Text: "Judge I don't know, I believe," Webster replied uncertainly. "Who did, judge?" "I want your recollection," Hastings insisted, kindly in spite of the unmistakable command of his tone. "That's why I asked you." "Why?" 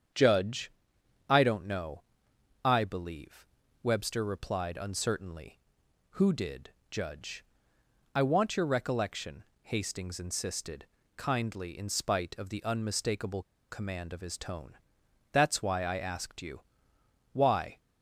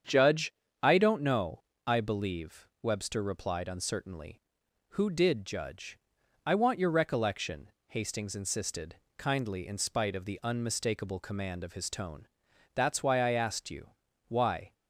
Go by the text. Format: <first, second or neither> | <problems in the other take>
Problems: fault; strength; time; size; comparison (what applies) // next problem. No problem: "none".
second | starts louder than the rest; strong; until 1.7 s; 8 dB; strong in the second // pauses between "Judge" and "I"; noticeable; at 0.7 s; 0.56 s long; slight in the second // pauses between "unmistakable" and "command"; slight; at 13.4 s; 0.25 s long